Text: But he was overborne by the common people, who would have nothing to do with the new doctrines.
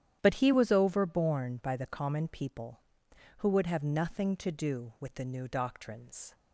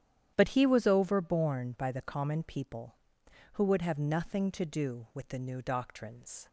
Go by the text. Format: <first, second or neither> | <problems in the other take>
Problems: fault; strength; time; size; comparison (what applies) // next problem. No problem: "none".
neither | starts louder than the rest; strong; the same in both